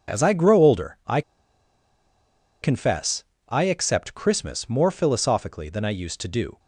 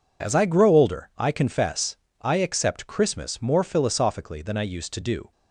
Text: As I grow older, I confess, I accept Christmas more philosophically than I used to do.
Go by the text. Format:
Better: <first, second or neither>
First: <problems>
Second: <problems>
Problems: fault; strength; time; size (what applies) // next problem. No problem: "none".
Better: second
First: pauses between "I" and "confess"; strong; at 1.2 s; 1.4 s long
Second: none